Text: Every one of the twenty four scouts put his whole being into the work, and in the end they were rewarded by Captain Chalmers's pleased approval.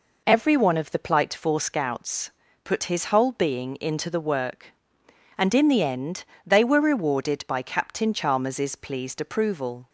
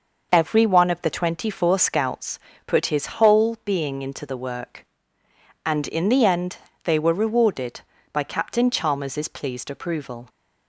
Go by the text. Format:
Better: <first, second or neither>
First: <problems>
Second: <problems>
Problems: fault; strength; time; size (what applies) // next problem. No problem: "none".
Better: second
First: says "plight" for "twenty"; at 1.0 s // pauses between "scouts" and "put"; slight; at 2.3 s; 0.32 s long // pauses between "end" and "they"; slight; at 6.2 s; 0.22 s long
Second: pauses between "scouts" and "put"; slight; at 2.3 s; 0.28 s long // pauses between "end" and "they"; slight; at 6.5 s; 0.26 s long